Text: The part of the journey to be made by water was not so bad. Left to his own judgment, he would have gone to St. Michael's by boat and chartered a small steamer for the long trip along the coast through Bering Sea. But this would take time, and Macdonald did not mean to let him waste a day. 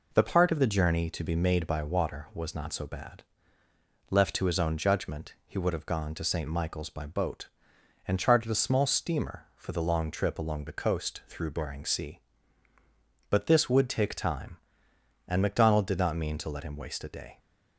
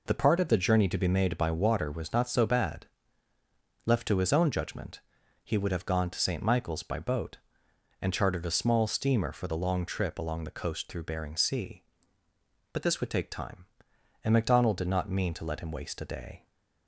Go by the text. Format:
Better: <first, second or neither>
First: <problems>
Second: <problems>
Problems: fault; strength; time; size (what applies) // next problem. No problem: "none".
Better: neither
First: none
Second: none